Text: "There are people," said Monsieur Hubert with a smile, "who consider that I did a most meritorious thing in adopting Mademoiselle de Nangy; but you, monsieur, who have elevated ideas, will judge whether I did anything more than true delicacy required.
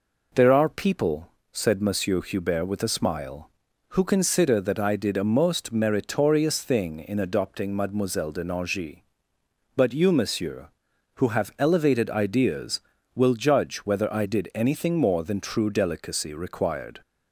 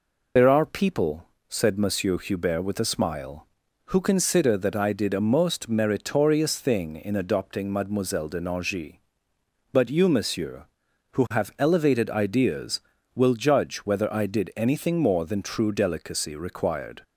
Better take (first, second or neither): first